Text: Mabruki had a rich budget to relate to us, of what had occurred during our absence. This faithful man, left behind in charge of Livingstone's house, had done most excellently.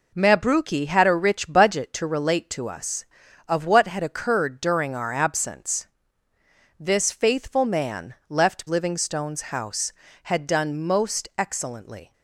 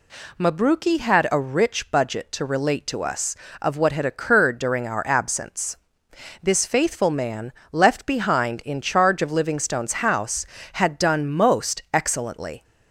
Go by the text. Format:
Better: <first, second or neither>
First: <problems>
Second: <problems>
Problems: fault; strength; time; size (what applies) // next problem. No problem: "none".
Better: second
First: skips "behind in charge of"; at 8.6 s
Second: none